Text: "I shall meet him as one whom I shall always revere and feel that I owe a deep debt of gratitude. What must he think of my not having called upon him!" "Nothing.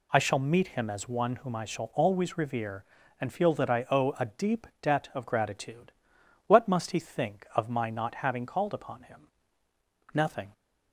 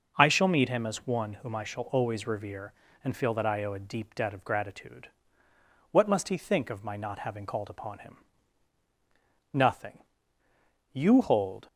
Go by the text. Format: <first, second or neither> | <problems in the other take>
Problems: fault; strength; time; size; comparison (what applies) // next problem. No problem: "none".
first | goes on to say "You hold"; noticeable; from 10.9 s on; 0.74 s long